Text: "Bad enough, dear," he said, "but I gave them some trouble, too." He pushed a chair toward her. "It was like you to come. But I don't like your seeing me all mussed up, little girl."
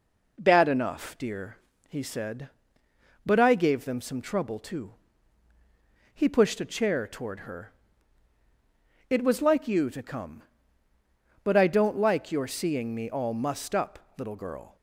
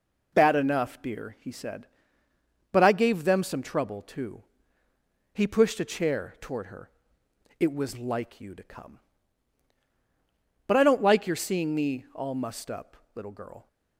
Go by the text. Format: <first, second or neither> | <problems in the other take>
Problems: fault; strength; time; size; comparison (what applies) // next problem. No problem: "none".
neither | none